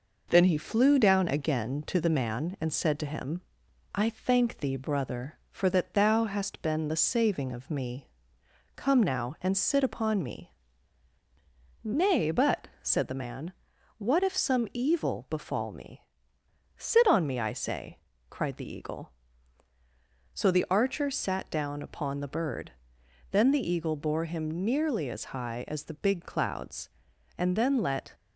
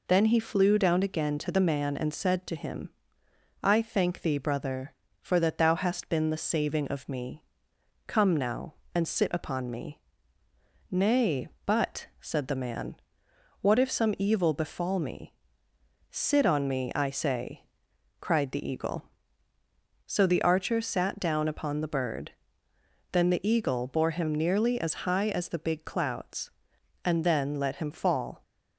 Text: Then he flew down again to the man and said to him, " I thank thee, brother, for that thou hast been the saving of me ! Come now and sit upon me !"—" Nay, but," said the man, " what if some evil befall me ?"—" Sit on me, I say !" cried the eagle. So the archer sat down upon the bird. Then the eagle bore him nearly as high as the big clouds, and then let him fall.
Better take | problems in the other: second | stops before "him fall"; at 28.1 s

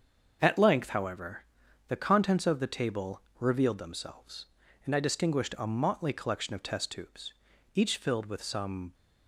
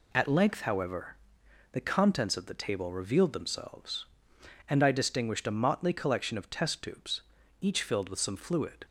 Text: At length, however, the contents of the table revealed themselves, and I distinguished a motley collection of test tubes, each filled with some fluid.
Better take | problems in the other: second | starts louder than the rest; until 1.4 s; 6.5 dB // pauses between "table" and "revealed"; slight; at 3.2 s; 0.20 s long // stops before "fluid"; at 8.9 s

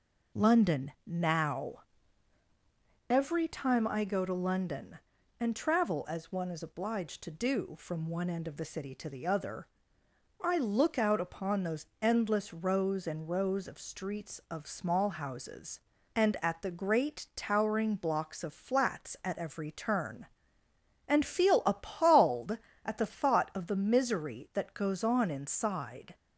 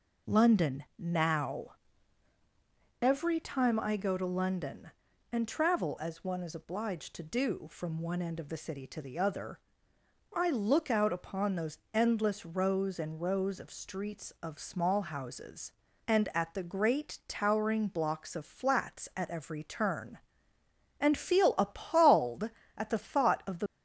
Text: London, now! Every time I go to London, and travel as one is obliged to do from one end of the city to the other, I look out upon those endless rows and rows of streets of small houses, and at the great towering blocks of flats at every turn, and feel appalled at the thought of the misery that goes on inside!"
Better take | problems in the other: first | pauses between "those" and "endless"; slight; at 11.7 s; 0.16 s long; slight in the first // stops before "misery that goes on inside"; at 23.6 s

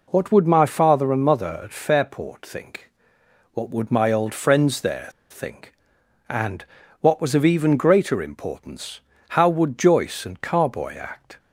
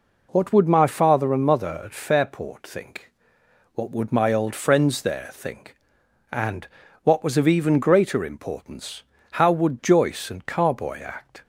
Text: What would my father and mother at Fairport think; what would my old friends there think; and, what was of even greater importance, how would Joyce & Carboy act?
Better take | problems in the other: second | pauses between "there" and "think"; slight; at 5.0 s; 0.20 s long

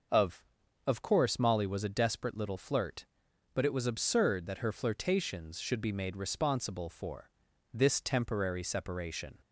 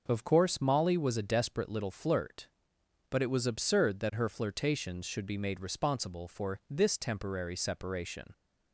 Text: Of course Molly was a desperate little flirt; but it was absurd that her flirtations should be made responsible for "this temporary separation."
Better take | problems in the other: second | starts louder than the rest; noticeable; until 1.5 s; 6 dB // says "Of" twice; at 0.8 s // pauses between "for" and "this"; at 7.3 s; 0.42 s long

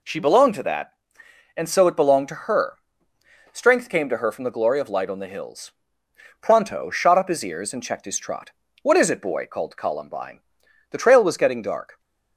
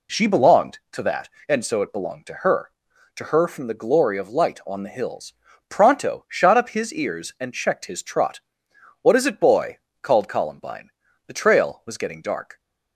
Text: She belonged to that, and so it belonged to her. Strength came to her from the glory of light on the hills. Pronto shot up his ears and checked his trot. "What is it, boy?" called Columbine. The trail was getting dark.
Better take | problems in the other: first | skips "Strength came"; at 2.9 s

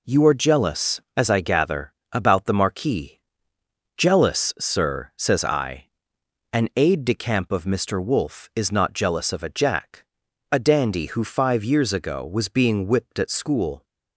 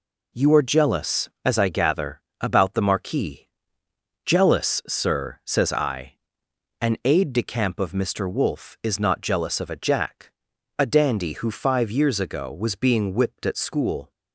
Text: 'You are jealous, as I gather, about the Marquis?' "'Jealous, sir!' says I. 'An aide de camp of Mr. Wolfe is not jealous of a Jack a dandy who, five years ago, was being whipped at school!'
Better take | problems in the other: neither | pauses between "Jack" and "a"; noticeable; the same in both

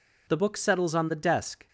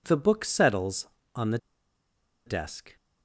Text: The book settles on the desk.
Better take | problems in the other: first | pauses between "the" and "desk"; noticeable; at 1.5 s; 0.88 s long

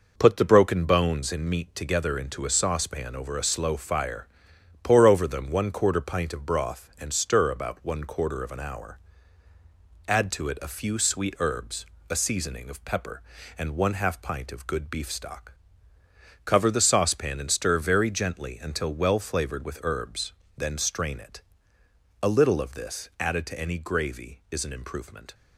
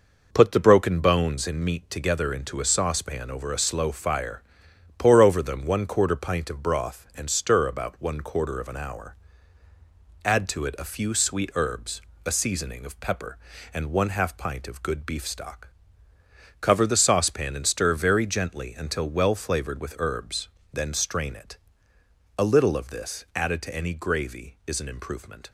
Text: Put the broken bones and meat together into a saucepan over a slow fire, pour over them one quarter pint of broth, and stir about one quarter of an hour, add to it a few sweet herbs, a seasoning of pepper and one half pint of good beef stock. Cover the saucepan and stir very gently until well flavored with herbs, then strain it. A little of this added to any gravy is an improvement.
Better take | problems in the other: neither | none

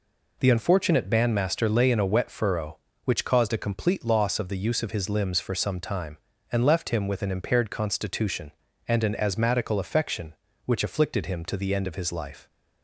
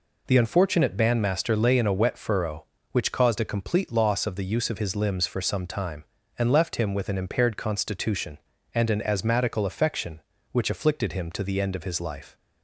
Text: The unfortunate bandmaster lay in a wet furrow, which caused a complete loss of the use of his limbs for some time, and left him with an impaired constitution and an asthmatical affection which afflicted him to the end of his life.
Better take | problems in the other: neither | none

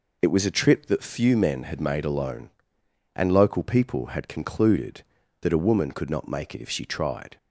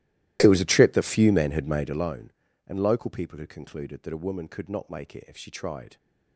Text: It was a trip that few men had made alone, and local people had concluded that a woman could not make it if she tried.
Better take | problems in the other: first | starts louder than the rest; strong; until 2.1 s; 15.5 dB

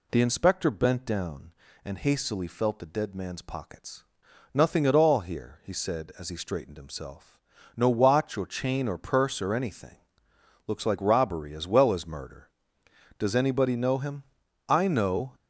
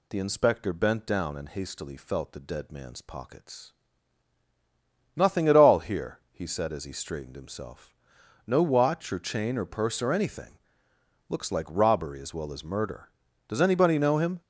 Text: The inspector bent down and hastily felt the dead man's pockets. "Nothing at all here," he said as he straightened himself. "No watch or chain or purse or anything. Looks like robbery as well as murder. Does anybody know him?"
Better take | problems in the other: second | goes on to say "I know"; noticeable; from 14.6 s on; 0.68 s long

